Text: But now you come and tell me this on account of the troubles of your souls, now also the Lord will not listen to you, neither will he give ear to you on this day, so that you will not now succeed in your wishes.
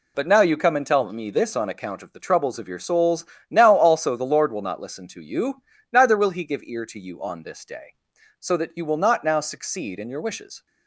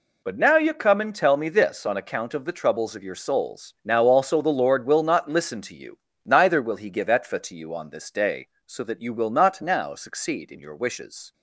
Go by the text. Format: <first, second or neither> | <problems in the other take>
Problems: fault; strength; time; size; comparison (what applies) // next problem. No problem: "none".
first | says "etfa" for "ear"; at 7.0 s